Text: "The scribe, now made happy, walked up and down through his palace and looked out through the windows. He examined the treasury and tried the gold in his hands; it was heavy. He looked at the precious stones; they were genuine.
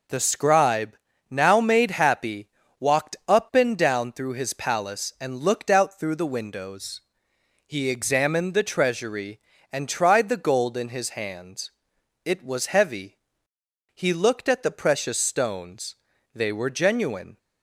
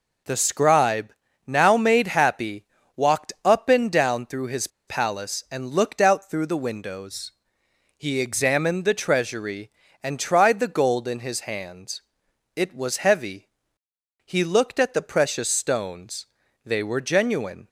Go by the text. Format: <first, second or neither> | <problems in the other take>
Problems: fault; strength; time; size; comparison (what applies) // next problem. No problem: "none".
first | pauses between "his" and "palace"; slight; at 4.6 s; 0.20 s long